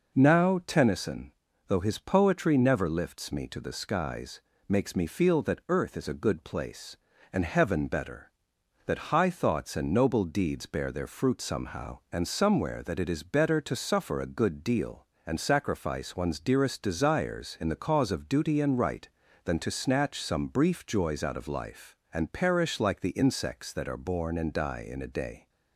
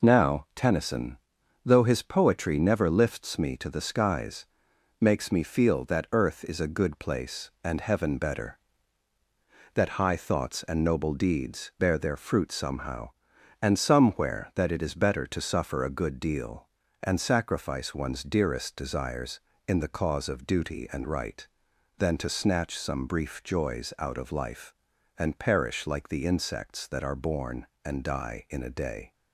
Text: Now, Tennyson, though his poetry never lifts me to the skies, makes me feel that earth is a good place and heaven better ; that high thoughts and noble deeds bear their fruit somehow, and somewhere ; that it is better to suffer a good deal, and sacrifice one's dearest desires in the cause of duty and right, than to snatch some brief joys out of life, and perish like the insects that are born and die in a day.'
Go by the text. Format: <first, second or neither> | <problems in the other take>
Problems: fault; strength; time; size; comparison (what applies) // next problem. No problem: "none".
neither | none